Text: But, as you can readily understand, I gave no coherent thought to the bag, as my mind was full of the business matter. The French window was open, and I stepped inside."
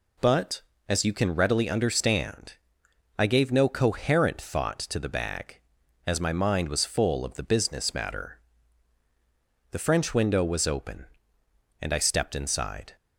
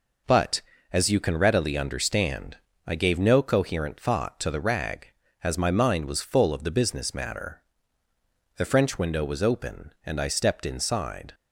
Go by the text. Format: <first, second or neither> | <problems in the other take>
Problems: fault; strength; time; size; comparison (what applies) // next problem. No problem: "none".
first | says "rag" for "bag"; at 4.5 s